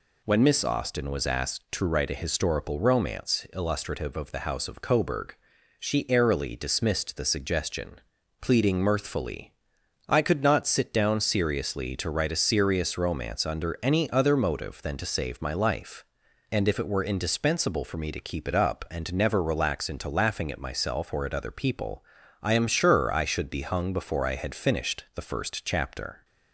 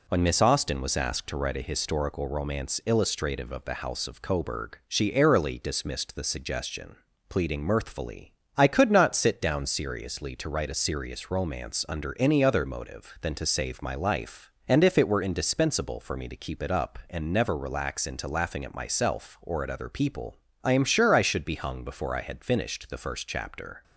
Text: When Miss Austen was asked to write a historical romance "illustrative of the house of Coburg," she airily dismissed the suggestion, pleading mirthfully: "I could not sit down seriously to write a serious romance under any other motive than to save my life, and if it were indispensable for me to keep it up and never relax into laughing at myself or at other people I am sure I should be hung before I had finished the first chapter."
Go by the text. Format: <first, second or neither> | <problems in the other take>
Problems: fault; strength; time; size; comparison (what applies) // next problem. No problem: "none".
neither | pauses between "people" and "I"; slight; the same in both